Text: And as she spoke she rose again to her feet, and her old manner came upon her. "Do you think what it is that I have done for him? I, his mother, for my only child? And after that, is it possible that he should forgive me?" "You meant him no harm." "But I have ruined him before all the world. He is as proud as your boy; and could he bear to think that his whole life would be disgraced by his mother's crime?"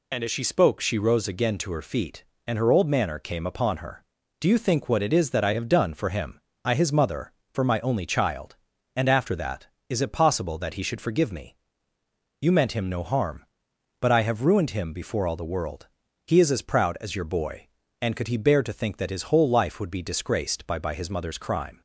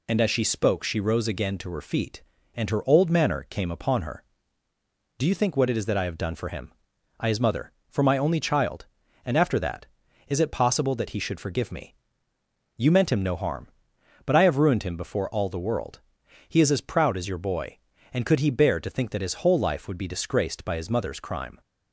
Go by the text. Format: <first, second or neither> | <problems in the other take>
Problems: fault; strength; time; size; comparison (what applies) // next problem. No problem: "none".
second | says "by" twice; at 20.7 s